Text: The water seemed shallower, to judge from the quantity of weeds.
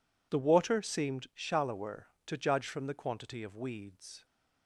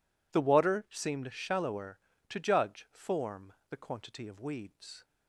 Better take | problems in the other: first | says "form" for "from"; at 2.8 s

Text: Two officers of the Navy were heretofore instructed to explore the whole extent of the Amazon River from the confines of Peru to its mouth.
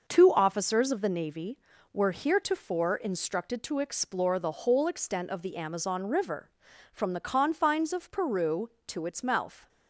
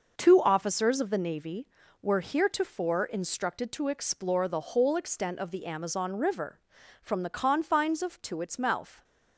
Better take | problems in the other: first | skips "Peru"; at 8.2 s

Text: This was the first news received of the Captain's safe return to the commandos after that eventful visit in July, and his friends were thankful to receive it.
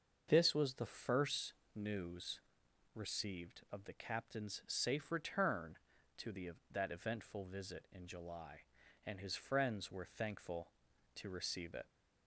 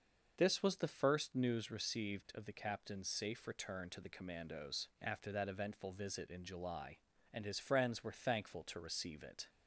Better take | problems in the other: second | starts louder than the rest; until 1.3 s; 6.5 dB; noticeable in the second // pauses between "first" and "news"; slight; at 1.5 s; 0.22 s long // pauses between "news" and "received"; noticeable; at 2.3 s; 0.54 s long // skips "commandos after"; at 6.5 s

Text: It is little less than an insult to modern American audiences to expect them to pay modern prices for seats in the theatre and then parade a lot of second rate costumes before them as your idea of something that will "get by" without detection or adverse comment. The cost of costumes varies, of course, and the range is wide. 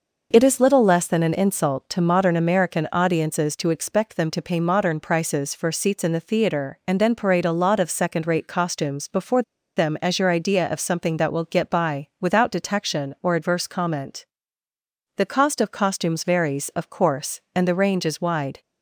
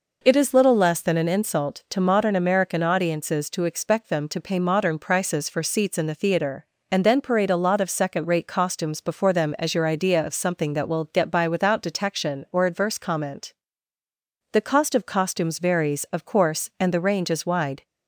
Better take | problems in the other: second | pauses between "before" and "them"; slight; at 9.4 s; 0.34 s long

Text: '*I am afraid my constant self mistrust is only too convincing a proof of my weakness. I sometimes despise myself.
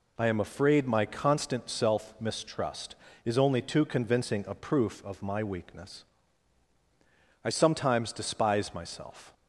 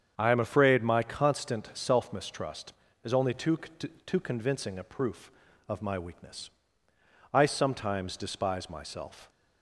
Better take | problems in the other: first | starts louder than the rest; strong; until 1.1 s; 7.5 dB // says "too" twice; at 3.5 s

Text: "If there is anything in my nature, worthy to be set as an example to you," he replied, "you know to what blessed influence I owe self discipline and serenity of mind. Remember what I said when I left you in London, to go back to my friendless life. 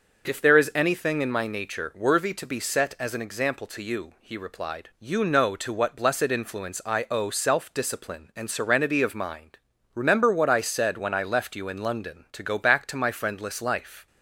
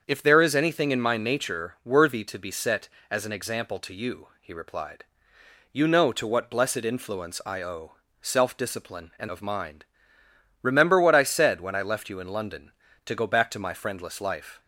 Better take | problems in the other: first | starts louder than the rest; until 1.0 s; 7 dB; also in the first // pauses between "owe" and "self"; slight; at 7.9 s; 0.24 s long // skips "serenity"; at 9.2 s

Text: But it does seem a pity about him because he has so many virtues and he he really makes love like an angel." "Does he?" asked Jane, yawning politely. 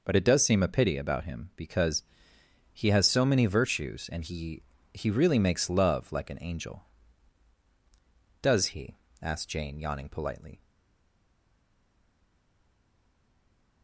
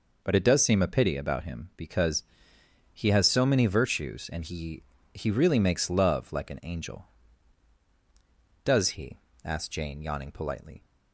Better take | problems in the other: second | pauses between "because" and "he"; noticeable; at 2.0 s; 0.68 s long; noticeable in the second // pauses between "he" and "he"; slight; at 4.6 s; 0.30 s long; slight in the second // stays silent after the last word; strong; from 10.6 s on; 3.2 s long

